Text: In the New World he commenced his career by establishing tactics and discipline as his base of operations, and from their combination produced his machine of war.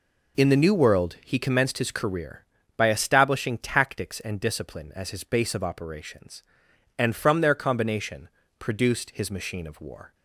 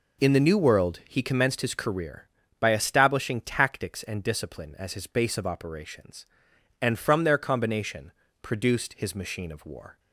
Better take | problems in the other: neither | pauses between "combination" and "produced"; slight; the same in both

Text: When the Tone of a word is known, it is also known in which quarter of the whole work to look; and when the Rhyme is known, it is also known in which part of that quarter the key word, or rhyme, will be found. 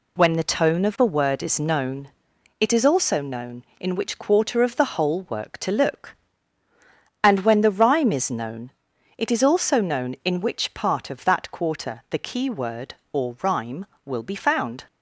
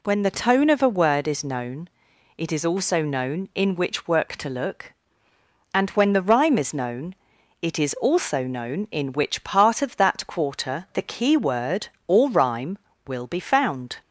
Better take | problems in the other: first | skips "quarter of the whole"; at 4.0 s

